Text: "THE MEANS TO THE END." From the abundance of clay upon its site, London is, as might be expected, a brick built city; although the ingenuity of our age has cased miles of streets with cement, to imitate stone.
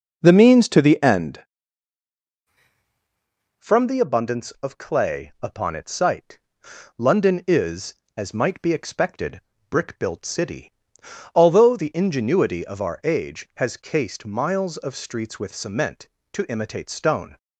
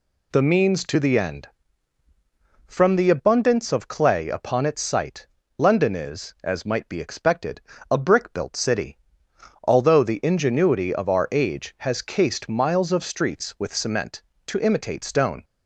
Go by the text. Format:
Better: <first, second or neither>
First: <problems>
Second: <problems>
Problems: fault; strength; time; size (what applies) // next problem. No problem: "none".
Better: second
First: skips "a"; at 9.5 s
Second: none